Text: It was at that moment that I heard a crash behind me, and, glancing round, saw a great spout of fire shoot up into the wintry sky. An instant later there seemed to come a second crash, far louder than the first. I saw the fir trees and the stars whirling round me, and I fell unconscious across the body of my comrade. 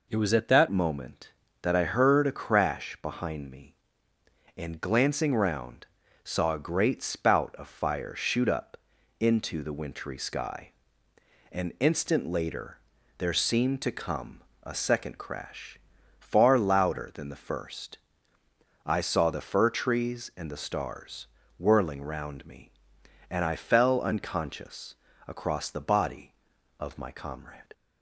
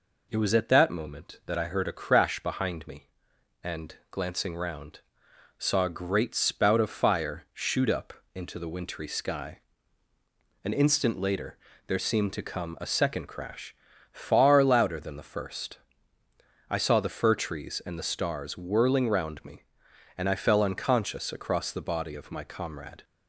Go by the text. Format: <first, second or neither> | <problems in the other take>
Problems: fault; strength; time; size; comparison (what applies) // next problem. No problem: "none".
second | changes voice at "moment"; from 0.7 s on; 27.0 s long // pauses between "up" and "into"; at 8.7 s; 0.42 s long; slight in the second // pauses between "later" and "there"; at 12.7 s; 0.40 s long; slight in the second // pauses between "come" and "a"; slight; at 14.4 s; 0.22 s long // pauses between "stars" and "whirling"; slight; at 21.2 s; 0.34 s long // pauses between "unconscious" and "across"; slight; at 24.9 s; 0.30 s long